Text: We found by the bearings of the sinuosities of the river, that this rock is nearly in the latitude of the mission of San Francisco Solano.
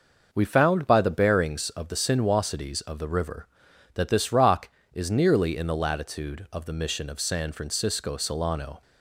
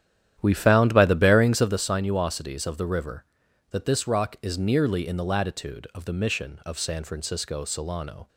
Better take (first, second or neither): first